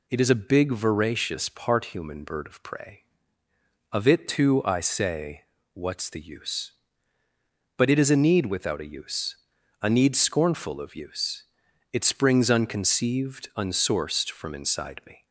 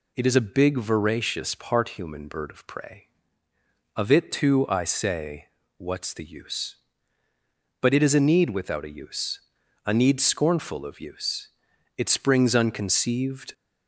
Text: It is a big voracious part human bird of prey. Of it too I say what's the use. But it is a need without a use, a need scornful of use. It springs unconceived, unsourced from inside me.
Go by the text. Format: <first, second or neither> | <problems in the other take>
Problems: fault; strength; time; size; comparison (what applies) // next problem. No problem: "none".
first | pauses between "say" and "what's"; slight; at 5.4 s; 0.32 s long; slight in the first // stops before "unsourced from inside me"; at 13.5 s